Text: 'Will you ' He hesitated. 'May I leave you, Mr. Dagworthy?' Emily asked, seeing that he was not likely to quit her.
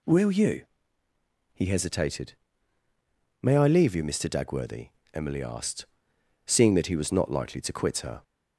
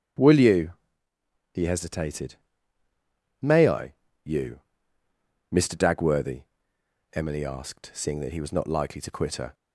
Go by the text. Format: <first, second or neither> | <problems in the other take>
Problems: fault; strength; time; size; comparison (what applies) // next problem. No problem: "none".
first | starts louder than the rest; strong; until 1.6 s; 7.5 dB // skips "leave"; at 4.0 s